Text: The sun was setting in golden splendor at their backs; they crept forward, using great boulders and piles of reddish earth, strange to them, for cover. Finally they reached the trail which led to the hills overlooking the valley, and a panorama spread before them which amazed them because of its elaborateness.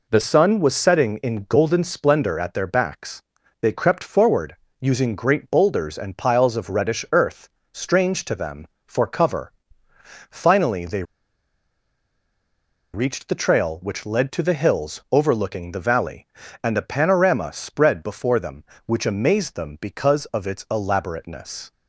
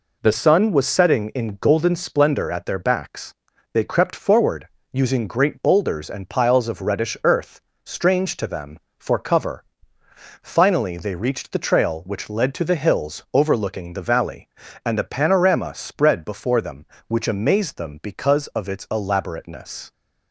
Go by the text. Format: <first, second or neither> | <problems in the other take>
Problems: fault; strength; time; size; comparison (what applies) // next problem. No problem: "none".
second | pauses between "they" and "reached"; strong; at 11.0 s; 1.9 s long